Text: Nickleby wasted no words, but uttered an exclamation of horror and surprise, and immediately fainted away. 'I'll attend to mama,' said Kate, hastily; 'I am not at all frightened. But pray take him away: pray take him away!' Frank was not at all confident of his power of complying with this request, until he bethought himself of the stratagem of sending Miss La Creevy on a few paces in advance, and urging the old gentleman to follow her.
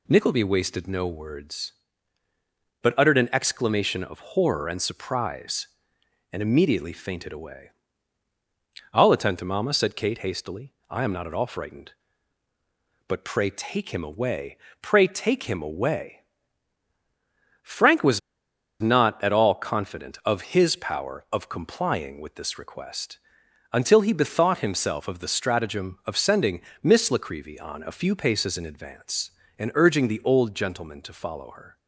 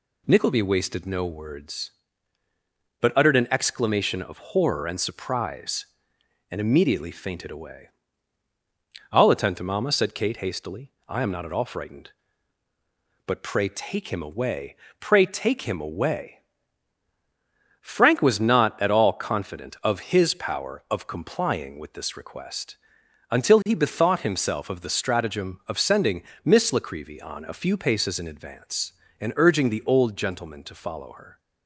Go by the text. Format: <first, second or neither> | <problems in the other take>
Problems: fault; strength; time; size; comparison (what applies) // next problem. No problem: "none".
second | pauses between "was" and "not"; noticeable; at 18.1 s; 0.61 s long // pauses between "sending" and "Miss"; slight; at 26.5 s; 0.22 s long; slight in the second